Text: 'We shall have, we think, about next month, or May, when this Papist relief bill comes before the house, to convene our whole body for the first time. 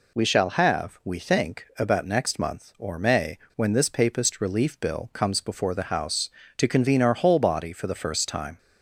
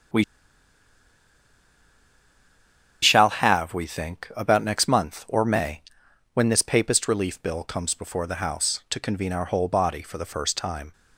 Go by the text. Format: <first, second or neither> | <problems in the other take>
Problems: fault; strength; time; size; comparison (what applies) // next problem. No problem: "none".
first | starts louder than the rest; strong; until 3.9 s; 8 dB // pauses between "We" and "shall"; strong; at 0.2 s; 2.7 s long